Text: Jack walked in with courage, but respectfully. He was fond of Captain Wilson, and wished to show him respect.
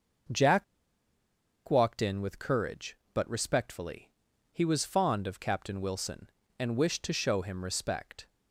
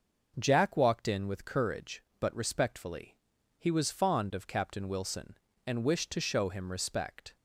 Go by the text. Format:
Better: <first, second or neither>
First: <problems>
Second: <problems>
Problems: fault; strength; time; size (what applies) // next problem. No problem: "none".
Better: second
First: pauses between "Jack" and "walked"; at 0.6 s; 1.0 s long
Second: none